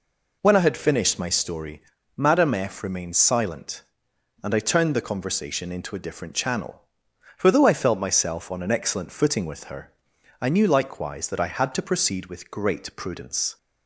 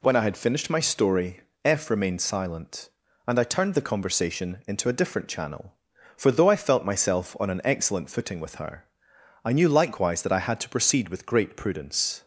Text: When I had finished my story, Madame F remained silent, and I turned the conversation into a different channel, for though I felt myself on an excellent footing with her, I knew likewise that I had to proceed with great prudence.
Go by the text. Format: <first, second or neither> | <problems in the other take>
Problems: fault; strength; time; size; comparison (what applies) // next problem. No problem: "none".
first | skips "Madame"; at 1.5 s